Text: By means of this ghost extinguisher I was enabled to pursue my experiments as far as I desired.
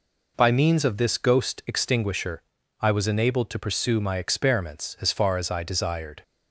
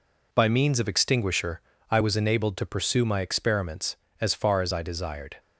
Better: first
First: pauses between "extinguisher" and "I"; at 2.4 s; 0.38 s long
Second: skips "this ghost"; at 0.8 s // pauses between "extinguisher" and "I"; slight; at 1.6 s; 0.30 s long

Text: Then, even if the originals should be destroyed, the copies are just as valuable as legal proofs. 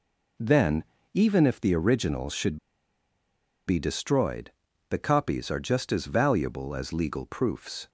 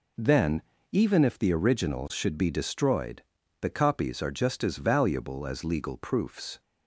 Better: second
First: pauses between "should" and "be"; at 2.5 s; 1.1 s long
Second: none

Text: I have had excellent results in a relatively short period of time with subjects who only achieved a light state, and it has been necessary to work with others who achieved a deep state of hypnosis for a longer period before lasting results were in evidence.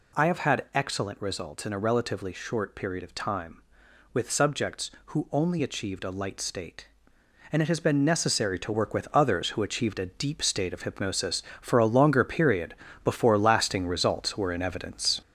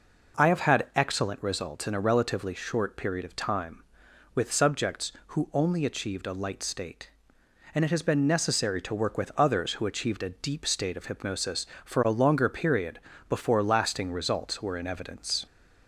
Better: second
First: gets louder; noticeable; throughout; 5 dB // pauses between "period" and "before"; slight; at 12.7 s; 0.30 s long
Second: pauses between "period" and "before"; slight; at 12.9 s; 0.30 s long

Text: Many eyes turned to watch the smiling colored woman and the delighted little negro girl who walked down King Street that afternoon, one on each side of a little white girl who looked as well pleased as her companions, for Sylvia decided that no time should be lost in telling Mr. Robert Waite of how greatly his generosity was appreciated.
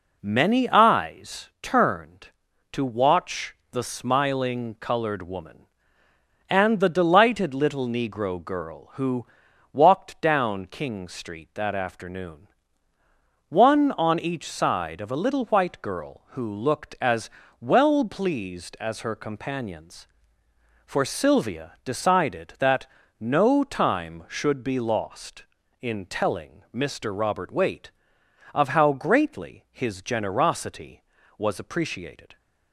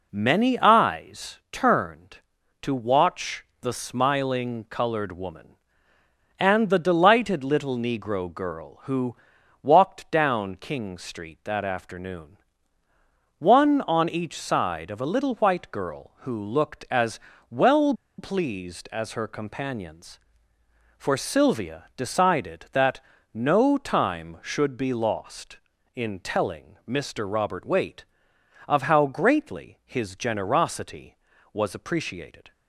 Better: first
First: pauses between "watch" and "the"; slight; at 3.5 s; 0.16 s long // pauses between "who" and "walked"; at 9.2 s; 0.44 s long // pauses between "as" and "well"; slight; at 17.2 s; 0.30 s long // pauses between "that" and "no"; slight; at 22.8 s; 0.34 s long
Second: pauses between "watch" and "the"; slight; at 3.4 s; 0.16 s long // pauses between "who" and "walked"; at 9.1 s; 0.44 s long // pauses between "as" and "well"; slight; at 17.1 s; 0.30 s long // pauses between "well" and "pleased"; slight; at 17.9 s; 0.25 s long // pauses between "that" and "no"; slight; at 22.9 s; 0.34 s long

